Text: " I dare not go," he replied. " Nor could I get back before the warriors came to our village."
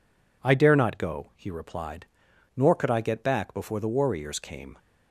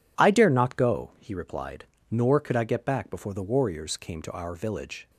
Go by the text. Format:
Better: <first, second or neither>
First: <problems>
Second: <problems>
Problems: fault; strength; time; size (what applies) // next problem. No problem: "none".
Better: second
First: stops before "to our village"; at 4.7 s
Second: none